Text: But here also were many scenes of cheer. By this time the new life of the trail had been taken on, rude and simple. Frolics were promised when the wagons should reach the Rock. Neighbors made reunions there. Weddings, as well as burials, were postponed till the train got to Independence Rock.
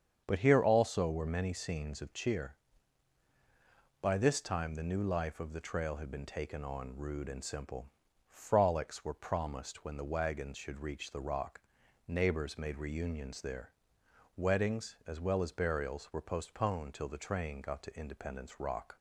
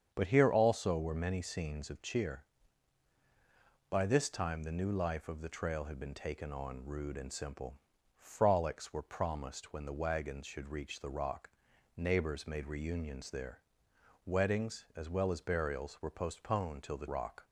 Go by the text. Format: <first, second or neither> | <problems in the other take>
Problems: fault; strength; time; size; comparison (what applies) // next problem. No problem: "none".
first | starts louder than the rest; strong; until 1.1 s; 8 dB; strong in the first // skips "train got to Independence"; at 17.0 s